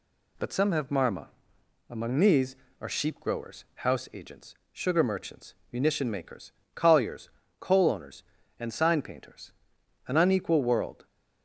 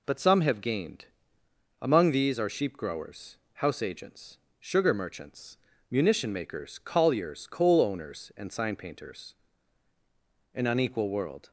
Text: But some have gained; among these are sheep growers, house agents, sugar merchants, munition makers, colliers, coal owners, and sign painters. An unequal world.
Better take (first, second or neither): second